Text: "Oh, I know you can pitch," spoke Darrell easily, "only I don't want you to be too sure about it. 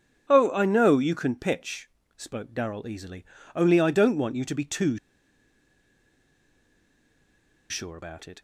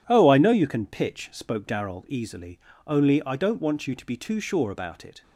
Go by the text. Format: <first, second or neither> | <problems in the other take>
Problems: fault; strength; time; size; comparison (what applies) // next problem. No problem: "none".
second | pauses between "too" and "sure"; strong; at 4.9 s; 2.7 s long